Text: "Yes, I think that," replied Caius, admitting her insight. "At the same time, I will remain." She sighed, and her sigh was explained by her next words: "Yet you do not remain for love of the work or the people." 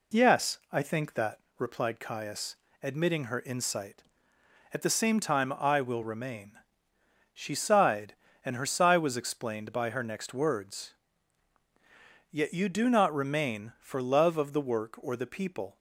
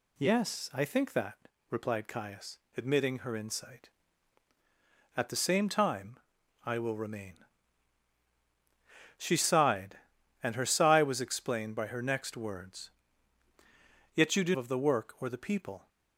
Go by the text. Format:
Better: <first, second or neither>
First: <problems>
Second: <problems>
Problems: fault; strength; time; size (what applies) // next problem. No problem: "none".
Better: first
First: none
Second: skips "not remain for love"; at 14.5 s